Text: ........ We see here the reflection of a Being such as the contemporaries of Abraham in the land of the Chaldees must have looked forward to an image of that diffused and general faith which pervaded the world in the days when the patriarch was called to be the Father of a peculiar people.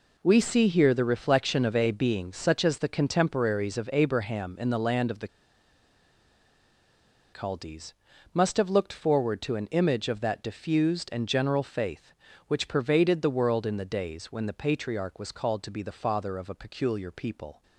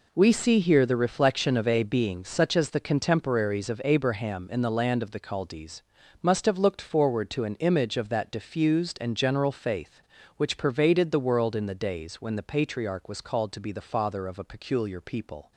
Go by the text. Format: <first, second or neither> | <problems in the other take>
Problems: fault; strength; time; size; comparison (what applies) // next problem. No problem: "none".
second | pauses between "the" and "Chaldees"; strong; at 5.2 s; 2.0 s long // pauses between "Chaldees" and "must"; at 7.9 s; 0.40 s long; also in the second